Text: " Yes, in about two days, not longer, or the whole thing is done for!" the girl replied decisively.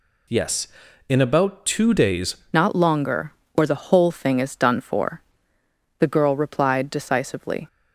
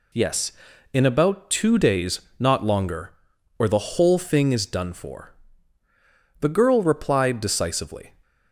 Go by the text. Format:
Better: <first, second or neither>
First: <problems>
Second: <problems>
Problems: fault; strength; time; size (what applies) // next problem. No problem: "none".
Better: second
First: changes voice at "not"; from 2.5 s on; 5.1 s long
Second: none